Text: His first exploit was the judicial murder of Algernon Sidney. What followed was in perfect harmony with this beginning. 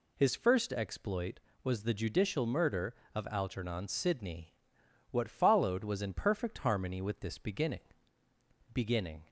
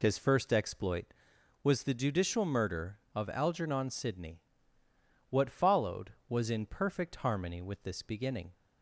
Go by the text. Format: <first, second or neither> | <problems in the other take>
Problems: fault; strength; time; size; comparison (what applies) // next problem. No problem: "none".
second | says "beginning" twice; at 8.7 s